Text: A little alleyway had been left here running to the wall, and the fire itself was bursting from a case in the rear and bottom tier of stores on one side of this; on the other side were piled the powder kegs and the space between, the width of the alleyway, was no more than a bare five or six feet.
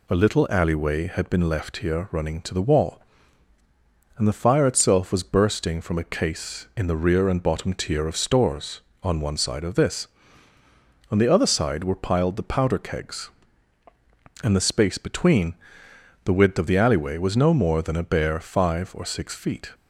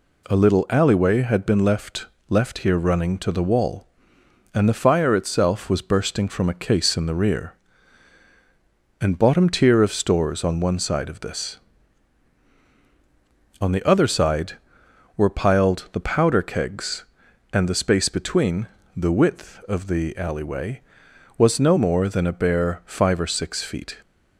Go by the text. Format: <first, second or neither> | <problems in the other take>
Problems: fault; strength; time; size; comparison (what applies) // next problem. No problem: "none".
first | says "left" twice; at 2.3 s